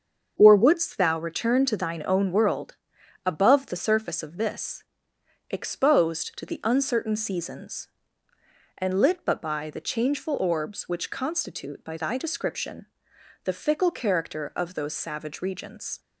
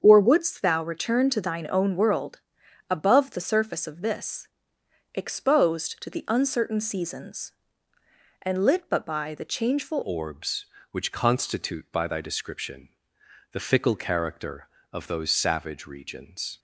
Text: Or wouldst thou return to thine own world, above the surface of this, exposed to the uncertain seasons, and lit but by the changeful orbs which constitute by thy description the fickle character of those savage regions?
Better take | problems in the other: first | starts louder than the rest; until 1.0 s; 7 dB; also in the first // changes voice at "orbs"; from 10.0 s on; 6.5 s long // pauses between "description" and "the"; noticeable; at 12.8 s; 0.64 s long; noticeable in the first

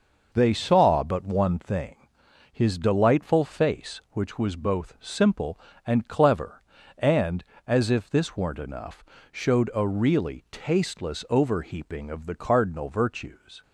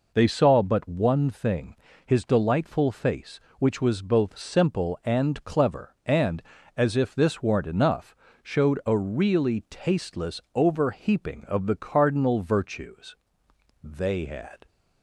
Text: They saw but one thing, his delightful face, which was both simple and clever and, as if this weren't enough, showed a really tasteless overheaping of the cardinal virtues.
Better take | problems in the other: first | goes on to say "They had"; noticeable; from 13.8 s on; 0.84 s long

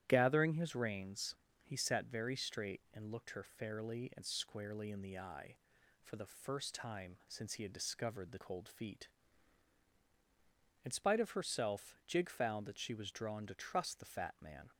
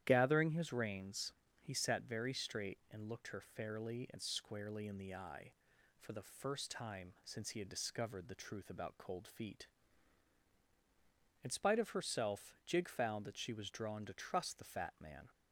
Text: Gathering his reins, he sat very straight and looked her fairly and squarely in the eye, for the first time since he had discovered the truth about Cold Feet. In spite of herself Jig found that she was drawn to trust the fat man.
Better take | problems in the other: second | starts louder than the rest; strong; until 1.0 s; 11.5 dB; strong in the second // skips "truth about"; at 8.3 s

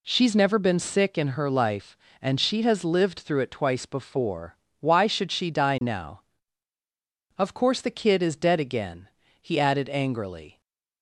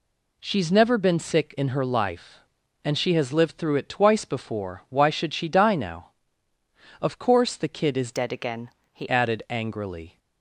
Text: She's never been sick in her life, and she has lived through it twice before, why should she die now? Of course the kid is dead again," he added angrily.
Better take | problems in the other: first | changes voice from "dead" to "he"; from 8.1 to 9.0 s; 0.9 s long

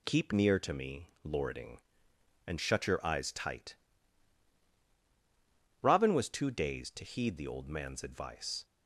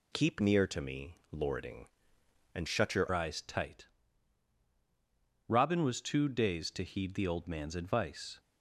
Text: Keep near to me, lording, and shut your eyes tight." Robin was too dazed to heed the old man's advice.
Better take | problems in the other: first | changes voice at "eyes"; from 3.1 s on; 5.2 s long

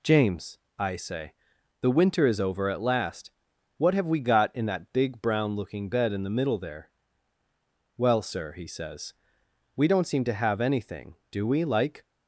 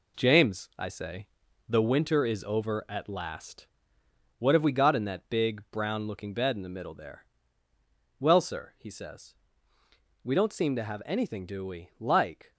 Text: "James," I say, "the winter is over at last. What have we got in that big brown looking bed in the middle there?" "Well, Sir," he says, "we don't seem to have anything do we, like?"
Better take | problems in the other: first | gets quieter; throughout; 6 dB

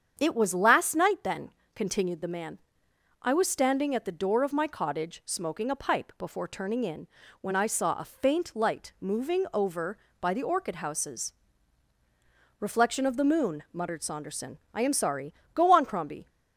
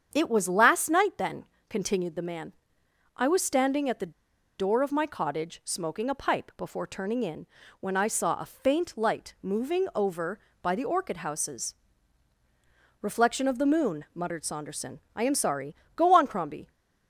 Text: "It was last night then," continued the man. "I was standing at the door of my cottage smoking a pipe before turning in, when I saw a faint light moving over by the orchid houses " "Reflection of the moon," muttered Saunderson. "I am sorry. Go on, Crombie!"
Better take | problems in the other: first | starts louder than the rest; strong; until 1.1 s; 7.5 dB; strong in the first // pauses between "the" and "door"; noticeable; at 4.1 s; 0.46 s long

